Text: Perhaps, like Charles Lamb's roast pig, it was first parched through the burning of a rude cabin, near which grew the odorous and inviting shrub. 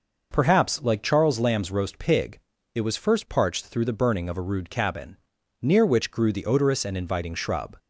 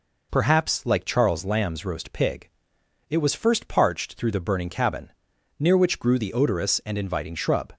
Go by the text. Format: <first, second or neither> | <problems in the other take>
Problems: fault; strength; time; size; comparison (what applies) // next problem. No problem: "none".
first | skips "of a rude"; at 4.6 s